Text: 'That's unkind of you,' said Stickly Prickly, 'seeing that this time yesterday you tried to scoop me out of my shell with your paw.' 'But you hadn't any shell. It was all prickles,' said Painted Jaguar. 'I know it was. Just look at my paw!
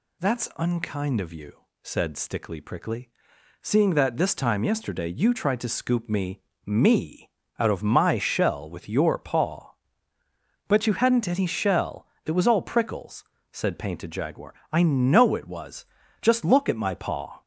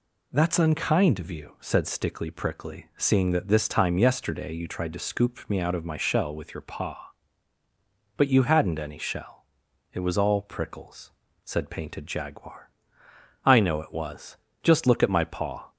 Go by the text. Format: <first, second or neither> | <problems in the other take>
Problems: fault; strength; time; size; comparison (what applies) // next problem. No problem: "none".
second | says "me" twice; at 6.6 s